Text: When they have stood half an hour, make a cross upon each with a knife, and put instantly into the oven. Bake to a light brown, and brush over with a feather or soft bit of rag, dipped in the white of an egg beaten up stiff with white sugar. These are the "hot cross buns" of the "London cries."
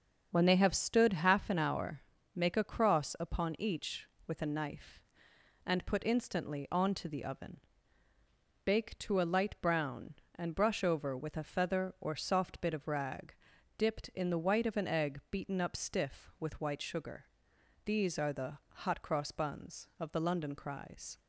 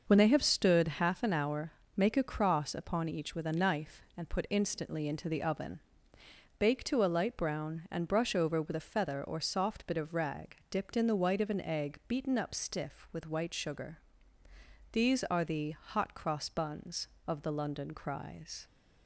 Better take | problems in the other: second | starts louder than the rest; until 1.3 s; 6.5 dB; noticeable in the second // says "onto" for "into"; at 6.7 s

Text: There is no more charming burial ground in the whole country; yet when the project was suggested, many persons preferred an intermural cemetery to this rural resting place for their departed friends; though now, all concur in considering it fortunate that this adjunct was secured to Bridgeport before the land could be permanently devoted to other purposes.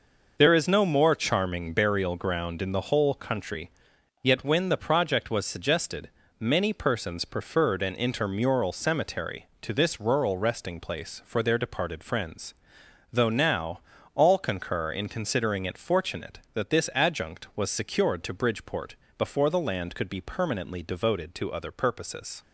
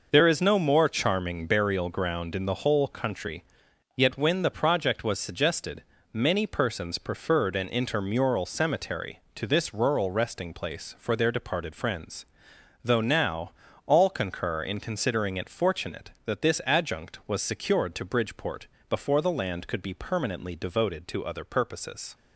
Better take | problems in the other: neither | pauses between "Bridgeport" and "before"; slight; the same in both

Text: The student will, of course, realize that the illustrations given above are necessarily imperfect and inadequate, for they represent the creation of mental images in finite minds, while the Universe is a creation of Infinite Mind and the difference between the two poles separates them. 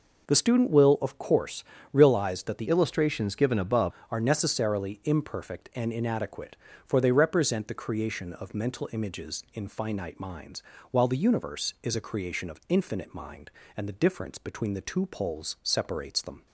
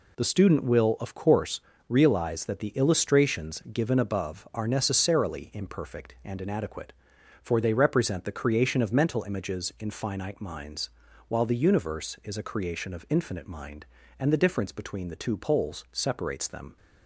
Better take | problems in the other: second | changes voice from "illustrations" to "above"; from 2.6 to 3.9 s; 1.3 s long

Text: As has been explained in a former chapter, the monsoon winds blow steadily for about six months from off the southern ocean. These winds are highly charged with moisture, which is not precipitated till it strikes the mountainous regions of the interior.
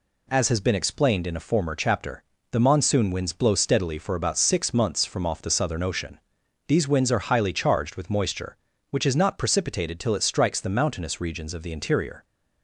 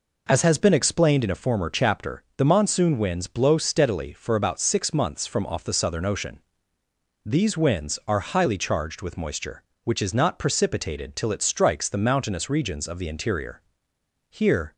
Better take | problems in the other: first | goes on to say "Here"; slight; from 14.2 s on; 0.44 s long

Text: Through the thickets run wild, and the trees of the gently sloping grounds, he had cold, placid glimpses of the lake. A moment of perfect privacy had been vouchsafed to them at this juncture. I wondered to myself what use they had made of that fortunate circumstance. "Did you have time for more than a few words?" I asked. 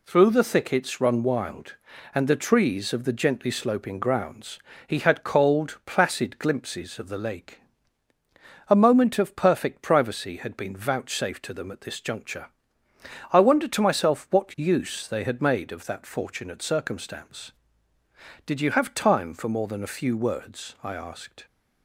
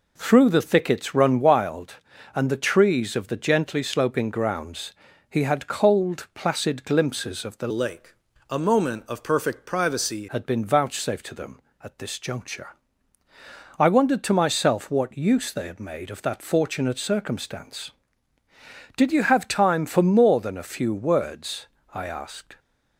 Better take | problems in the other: first | changes voice from "lake" to "privacy"; from 7.7 to 10.2 s; 2.5 s long

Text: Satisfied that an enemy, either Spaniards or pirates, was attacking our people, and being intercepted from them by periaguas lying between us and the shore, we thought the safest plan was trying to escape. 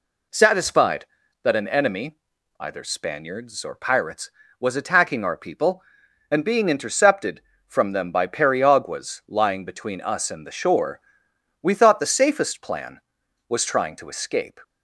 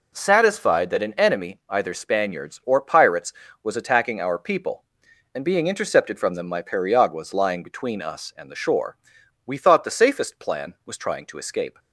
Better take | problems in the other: first | says "my" for "by"; at 6.4 s

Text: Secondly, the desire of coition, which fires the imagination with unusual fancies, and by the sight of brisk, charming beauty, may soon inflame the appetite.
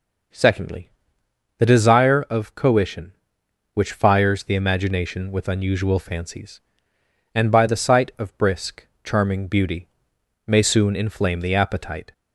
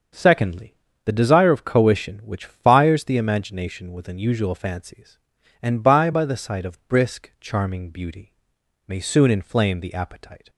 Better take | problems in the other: first | starts louder than the rest; until 1.4 s; 6.5 dB // says "by" twice; at 6.1 s

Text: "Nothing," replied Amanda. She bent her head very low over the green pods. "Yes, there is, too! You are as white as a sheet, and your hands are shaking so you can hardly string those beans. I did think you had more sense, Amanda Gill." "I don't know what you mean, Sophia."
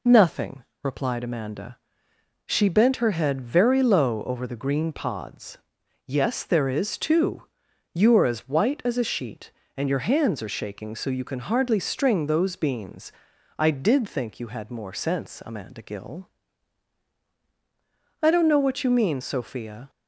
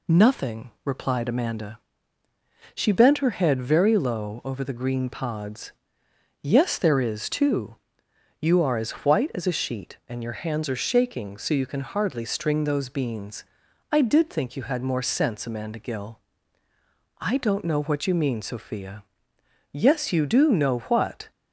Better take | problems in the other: first | goes on to say "Yes you do know what"; from 19.7 s on; 1.5 s long

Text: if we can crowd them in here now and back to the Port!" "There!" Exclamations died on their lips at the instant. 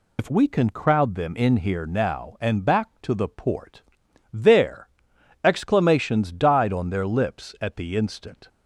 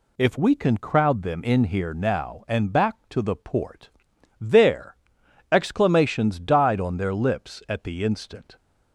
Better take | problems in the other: second | loses the start of "if"; at 0.1 s; 90 ms

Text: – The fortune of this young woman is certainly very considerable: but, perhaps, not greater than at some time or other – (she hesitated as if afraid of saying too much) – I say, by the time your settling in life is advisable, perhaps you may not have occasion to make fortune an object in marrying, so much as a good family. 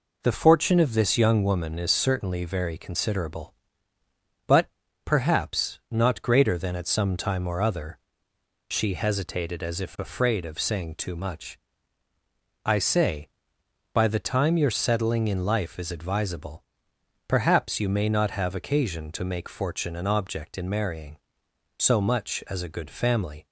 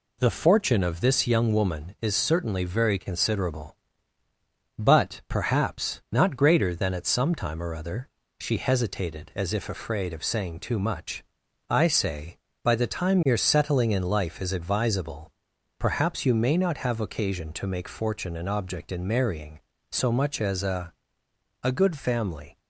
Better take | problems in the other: first | says "a" twice; at 21.6 s

